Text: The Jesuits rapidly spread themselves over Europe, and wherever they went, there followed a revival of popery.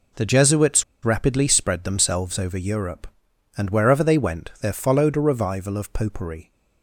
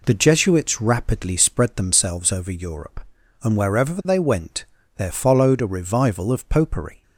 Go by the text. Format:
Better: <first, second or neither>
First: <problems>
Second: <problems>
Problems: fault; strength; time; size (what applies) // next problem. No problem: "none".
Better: second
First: pauses between "Jesuits" and "rapidly"; slight; at 0.8 s; 0.19 s long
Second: none